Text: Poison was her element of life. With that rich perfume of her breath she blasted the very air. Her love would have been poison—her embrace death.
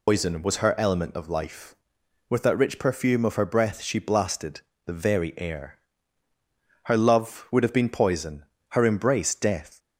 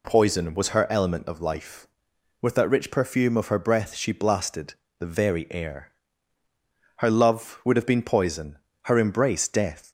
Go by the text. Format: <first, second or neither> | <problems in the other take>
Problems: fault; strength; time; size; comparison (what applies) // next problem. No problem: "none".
second | loses the start of "Poison"; at 0.0 s; 150 ms // pauses between "blasted" and "the"; slight; at 4.6 s; 0.26 s long; slight in the second